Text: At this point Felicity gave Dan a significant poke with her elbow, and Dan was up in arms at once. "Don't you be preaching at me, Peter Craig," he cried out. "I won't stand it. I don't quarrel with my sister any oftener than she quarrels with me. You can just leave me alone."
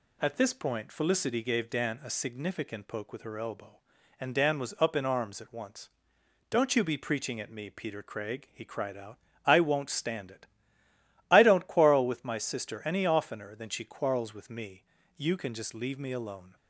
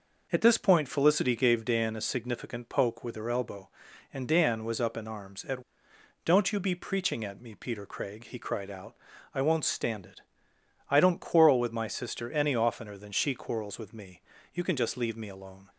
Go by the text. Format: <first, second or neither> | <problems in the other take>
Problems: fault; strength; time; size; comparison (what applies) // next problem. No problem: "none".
first | skips "once"; at 5.9 s